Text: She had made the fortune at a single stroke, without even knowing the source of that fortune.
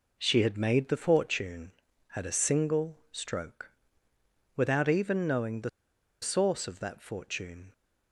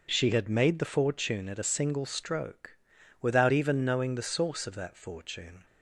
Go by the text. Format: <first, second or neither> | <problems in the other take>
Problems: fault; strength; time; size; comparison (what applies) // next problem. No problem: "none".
second | pauses between "the" and "source"; noticeable; at 5.6 s; 0.52 s long